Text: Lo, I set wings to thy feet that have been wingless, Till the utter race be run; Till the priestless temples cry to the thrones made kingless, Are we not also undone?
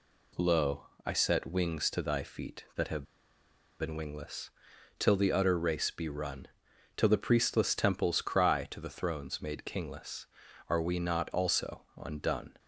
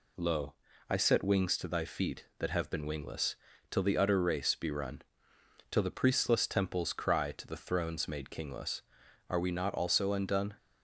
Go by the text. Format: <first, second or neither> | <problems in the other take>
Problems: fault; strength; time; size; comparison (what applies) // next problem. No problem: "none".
second | pauses between "have" and "been"; noticeable; at 3.0 s; 0.76 s long // pauses between "also" and "undone"; slight; at 11.8 s; 0.16 s long